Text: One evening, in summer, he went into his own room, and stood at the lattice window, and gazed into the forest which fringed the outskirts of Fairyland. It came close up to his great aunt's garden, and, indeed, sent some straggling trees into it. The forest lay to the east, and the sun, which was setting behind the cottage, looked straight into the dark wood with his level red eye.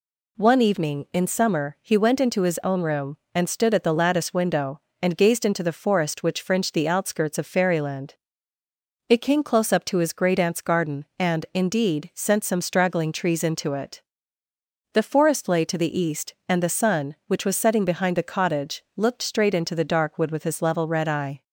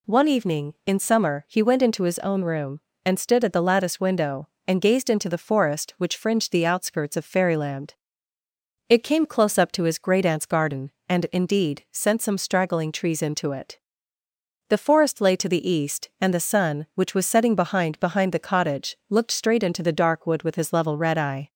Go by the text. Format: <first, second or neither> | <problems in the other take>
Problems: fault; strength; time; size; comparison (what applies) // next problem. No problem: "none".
first | says "behind" twice; at 17.9 s